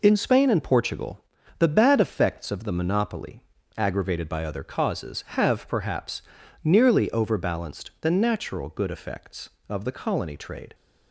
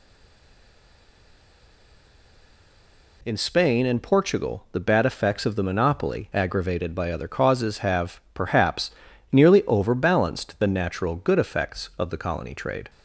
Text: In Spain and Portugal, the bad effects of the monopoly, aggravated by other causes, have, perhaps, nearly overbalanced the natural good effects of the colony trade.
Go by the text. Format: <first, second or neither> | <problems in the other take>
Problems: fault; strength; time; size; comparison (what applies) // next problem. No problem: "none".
first | stays silent before the first word; strong; until 3.2 s; 3.2 s long